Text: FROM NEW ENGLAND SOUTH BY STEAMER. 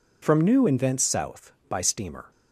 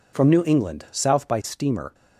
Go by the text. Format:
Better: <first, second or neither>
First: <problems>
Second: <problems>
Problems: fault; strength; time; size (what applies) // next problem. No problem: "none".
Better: second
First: says "Invents" for "ENGLAND"; at 0.6 s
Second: none